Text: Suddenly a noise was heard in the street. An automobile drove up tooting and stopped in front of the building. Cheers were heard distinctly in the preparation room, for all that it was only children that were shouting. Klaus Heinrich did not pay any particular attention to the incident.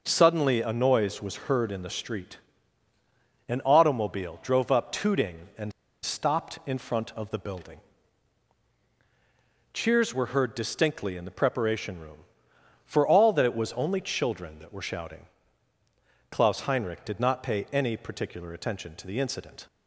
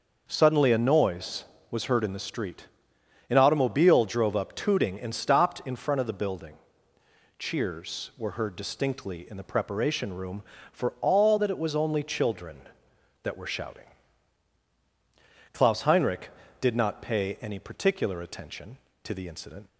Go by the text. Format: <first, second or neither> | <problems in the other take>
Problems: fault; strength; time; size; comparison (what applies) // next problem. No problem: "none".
second | pauses between "and" and "stopped"; slight; at 5.7 s; 0.32 s long